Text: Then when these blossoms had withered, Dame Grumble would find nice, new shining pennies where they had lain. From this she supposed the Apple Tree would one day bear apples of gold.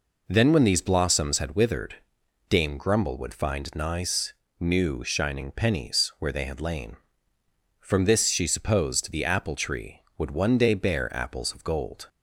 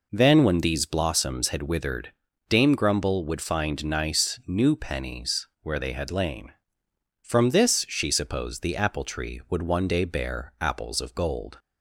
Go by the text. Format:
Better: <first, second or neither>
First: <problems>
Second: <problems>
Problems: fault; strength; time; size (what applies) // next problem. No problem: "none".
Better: first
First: none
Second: skips "shining"; at 4.7 s // pauses between "pennies" and "where"; slight; at 5.4 s; 0.16 s long